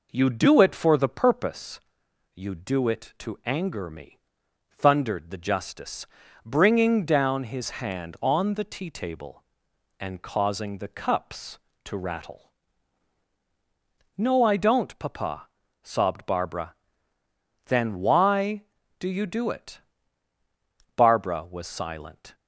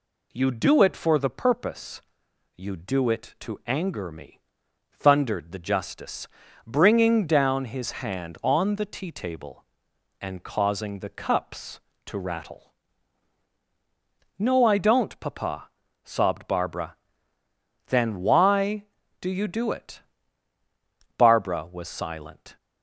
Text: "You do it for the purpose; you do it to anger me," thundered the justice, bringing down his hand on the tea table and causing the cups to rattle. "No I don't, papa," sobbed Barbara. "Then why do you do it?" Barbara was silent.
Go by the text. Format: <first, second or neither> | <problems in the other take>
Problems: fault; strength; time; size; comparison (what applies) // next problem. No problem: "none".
second | starts louder than the rest; noticeable; until 1.6 s; 4.5 dB